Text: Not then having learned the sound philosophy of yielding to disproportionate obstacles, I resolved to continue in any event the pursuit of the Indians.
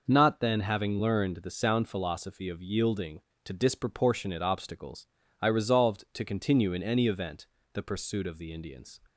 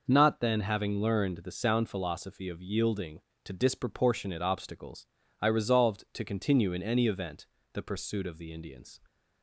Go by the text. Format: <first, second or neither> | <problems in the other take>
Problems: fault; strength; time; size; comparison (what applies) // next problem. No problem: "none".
neither | pauses between "event" and "the"; slight; the same in both